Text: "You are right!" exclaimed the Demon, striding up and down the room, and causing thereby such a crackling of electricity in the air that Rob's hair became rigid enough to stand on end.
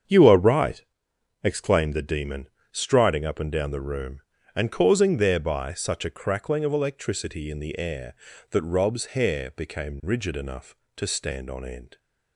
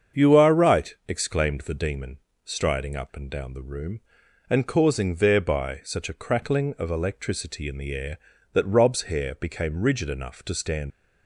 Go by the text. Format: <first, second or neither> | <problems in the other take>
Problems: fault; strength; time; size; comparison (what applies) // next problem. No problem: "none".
first | starts louder than the rest; strong; until 1.3 s; 7 dB; strong in the first // stops before "on end"; at 10.9 s